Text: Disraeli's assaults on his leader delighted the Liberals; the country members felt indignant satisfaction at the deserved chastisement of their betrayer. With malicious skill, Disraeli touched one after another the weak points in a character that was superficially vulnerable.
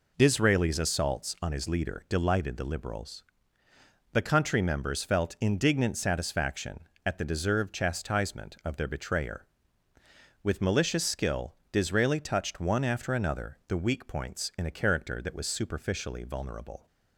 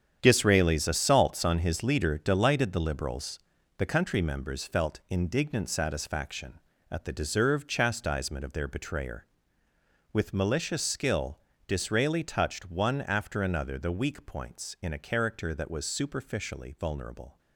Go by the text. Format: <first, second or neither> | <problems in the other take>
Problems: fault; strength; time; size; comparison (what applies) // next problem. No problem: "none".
first | gets quieter; strong; throughout; 10 dB